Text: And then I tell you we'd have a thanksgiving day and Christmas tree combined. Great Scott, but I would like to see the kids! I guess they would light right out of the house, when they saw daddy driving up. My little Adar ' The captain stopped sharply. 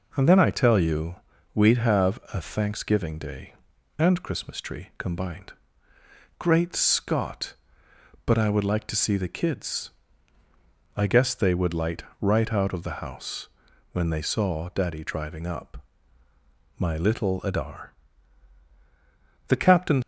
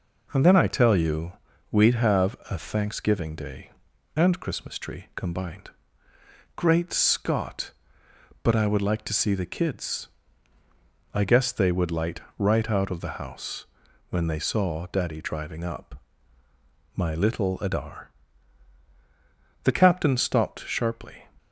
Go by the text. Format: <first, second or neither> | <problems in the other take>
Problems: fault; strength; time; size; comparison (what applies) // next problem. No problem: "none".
second | pauses between "you" and "we'd"; at 1.1 s; 0.38 s long; also in the second // pauses between "light" and "right"; slight; at 12.0 s; 0.16 s long; slight in the second // stops before "stopped sharply"; at 20.0 s